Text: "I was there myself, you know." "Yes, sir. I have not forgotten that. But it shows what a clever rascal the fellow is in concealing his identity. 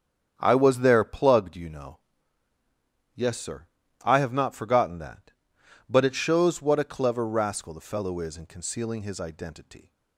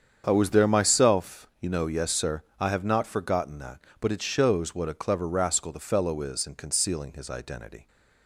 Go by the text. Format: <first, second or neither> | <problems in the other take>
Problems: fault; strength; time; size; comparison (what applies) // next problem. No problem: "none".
second | starts louder than the rest; strong; until 1.3 s; 8.5 dB; strong in the second // says "plugged" for "myself"; at 1.0 s